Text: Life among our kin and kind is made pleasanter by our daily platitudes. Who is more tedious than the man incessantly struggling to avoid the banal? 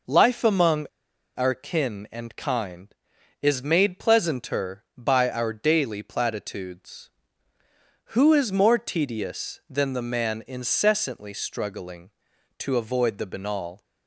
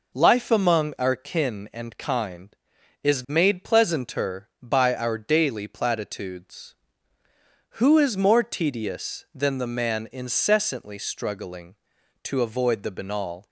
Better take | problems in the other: second | pauses between "among" and "our"; noticeable; at 0.8 s; 0.49 s long

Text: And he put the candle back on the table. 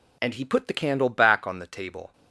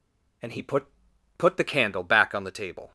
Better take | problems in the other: first | says "put" twice; at 1.3 s

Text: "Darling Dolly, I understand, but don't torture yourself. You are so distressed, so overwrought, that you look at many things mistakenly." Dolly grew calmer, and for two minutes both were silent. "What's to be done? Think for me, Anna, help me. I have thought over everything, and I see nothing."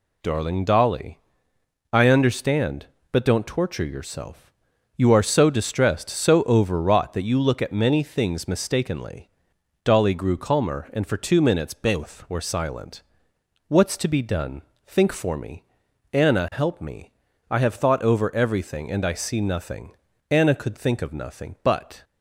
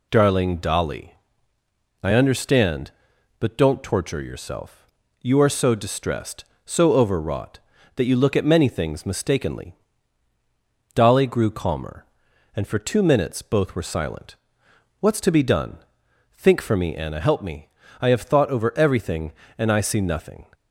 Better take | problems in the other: second | goes on to say "Anna could think of nothing but"; strong; from 20.2 s on; 1.7 s long

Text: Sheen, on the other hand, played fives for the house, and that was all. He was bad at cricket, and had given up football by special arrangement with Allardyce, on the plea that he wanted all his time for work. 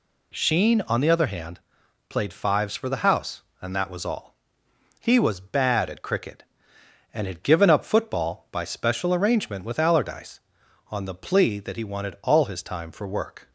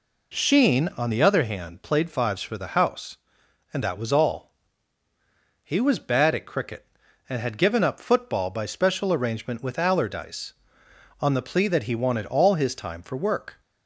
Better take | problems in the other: neither | none

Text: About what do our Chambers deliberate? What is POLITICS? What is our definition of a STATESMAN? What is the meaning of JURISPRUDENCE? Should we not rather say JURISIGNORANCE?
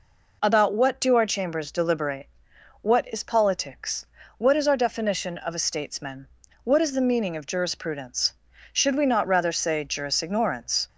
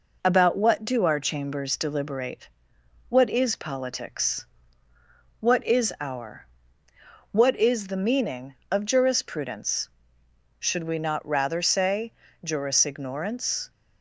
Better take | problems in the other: first | skips "definition of a STATESMAN"; at 6.8 s // pauses between "say" and "JURISIGNORANCE"; slight; at 12.1 s; 0.32 s long

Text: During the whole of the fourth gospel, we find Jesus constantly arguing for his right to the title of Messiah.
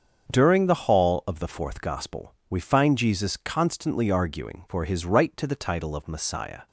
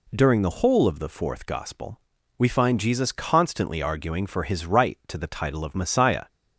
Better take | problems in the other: second | starts louder than the rest; until 1.3 s; 7 dB // says "hall" for "whole"; at 0.8 s

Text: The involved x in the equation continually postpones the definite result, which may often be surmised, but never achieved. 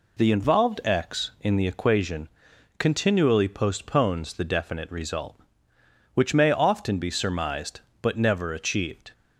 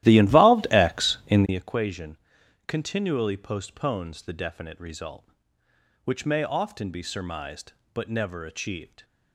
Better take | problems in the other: first | starts louder than the rest; strong; until 1.6 s; 14.5 dB // pauses between "equation" and "continually"; noticeable; at 2.1 s; 0.52 s long; noticeable in the first

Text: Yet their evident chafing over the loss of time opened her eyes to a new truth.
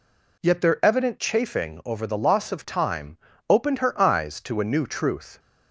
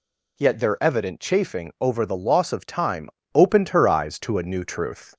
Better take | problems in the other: neither | pauses between "time" and "opened"; slight; the same in both

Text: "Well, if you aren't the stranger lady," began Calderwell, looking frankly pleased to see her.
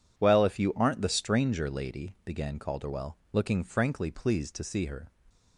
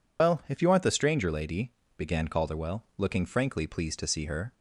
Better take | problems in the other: first | loses the start of "Well"; at 0.1 s; 100 ms

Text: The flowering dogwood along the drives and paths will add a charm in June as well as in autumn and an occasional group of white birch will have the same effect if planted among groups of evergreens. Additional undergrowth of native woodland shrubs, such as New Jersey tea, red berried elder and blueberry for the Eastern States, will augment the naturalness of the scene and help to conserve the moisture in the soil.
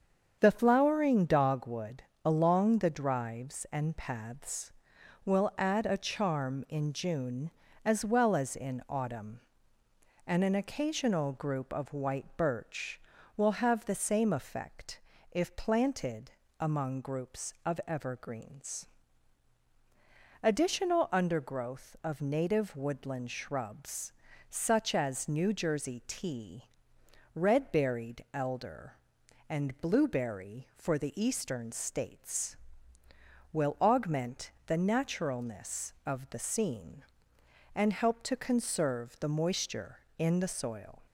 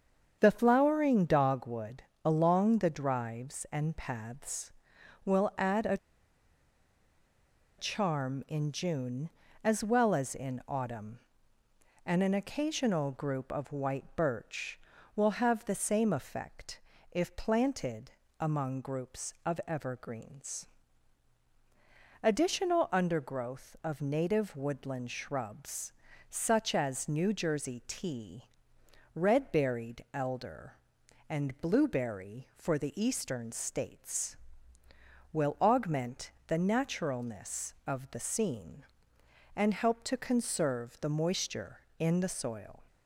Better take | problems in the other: first | starts louder than the rest; strong; until 1.4 s; 7.5 dB; strong in the first // pauses between "dogwood" and "along"; slight; at 2.0 s; 0.20 s long; slight in the first // pauses between "a" and "charm"; strong; at 5.9 s; 1.8 s long // pauses between "effect" and "if"; slight; at 16.7 s; 0.32 s long; slight in the first // pauses between "planted" and "among"; slight; at 18.1 s; 0.28 s long; slight in the first // pauses between "augment" and "the"; slight; at 36.2 s; 0.16 s long; slight in the first

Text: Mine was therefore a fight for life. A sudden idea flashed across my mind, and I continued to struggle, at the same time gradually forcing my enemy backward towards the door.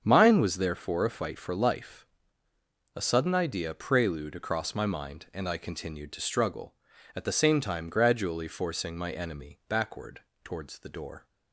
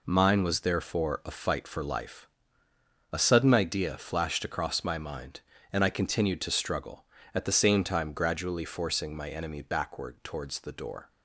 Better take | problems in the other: second | starts louder than the rest; until 1.0 s; 7 dB // says "prelude" for "flashed"; at 3.7 s // pauses between "backward" and "towards"; slight; at 10.2 s; 0.20 s long

